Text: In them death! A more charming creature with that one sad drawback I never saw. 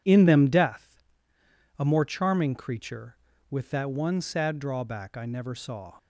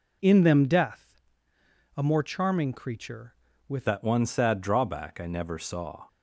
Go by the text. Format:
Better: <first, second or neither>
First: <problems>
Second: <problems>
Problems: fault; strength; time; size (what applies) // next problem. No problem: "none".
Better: first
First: none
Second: changes voice at "that"; from 3.8 s on; 2.2 s long